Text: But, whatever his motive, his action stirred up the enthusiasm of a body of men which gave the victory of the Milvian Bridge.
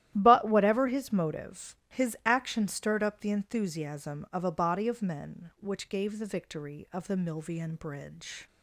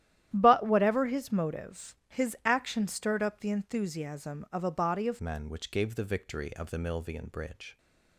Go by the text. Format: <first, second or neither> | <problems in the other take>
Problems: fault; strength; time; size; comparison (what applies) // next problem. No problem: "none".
first | starts louder than the rest; strong; until 1.3 s; 12 dB; strong in the first // changes voice at "men"; from 5.1 s on; 2.6 s long